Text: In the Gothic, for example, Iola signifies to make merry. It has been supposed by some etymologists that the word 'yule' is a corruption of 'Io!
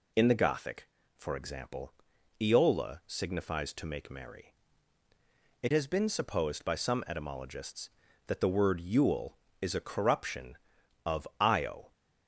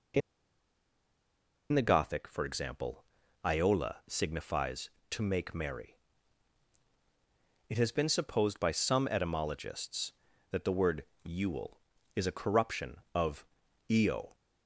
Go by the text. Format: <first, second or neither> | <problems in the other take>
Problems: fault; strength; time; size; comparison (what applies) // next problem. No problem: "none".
first | pauses between "In" and "the"; strong; at 0.2 s; 1.5 s long // pauses between "word" and "yule"; slight; at 11.0 s; 0.18 s long // pauses between "of" and "Io"; at 13.4 s; 0.42 s long